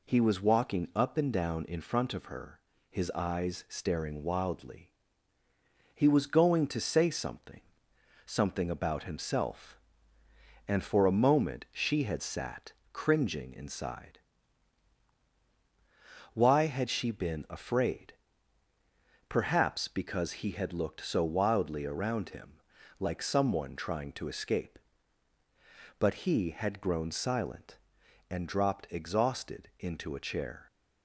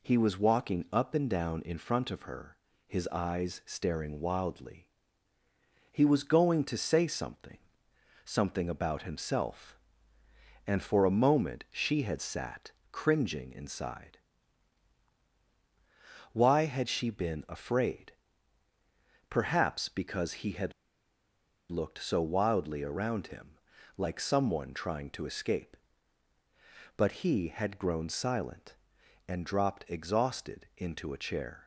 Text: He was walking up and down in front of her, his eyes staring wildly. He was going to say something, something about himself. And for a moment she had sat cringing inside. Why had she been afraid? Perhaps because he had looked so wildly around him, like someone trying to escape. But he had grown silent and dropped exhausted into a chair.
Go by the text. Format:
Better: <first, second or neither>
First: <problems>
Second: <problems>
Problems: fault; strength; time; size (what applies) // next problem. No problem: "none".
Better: first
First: pauses between "sat" and "cringing"; slight; at 12.7 s; 0.22 s long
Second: pauses between "sat" and "cringing"; slight; at 12.7 s; 0.22 s long // pauses between "had" and "looked"; at 20.7 s; 0.98 s long